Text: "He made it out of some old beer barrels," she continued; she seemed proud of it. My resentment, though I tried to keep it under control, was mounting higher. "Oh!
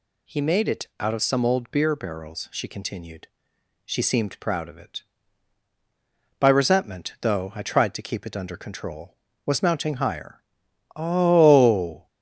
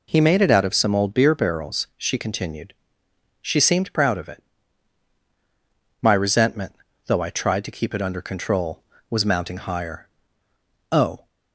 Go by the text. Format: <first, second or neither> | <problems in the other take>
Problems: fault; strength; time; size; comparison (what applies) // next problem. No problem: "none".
second | says "By" for "My"; at 6.3 s